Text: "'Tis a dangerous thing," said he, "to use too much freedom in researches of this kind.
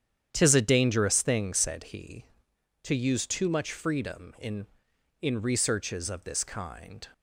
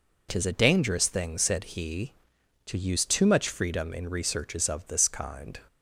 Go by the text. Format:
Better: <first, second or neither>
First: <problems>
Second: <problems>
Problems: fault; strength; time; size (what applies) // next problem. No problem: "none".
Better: second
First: starts louder than the rest; strong; until 1.3 s; 9 dB // says "in" twice; at 5.2 s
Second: none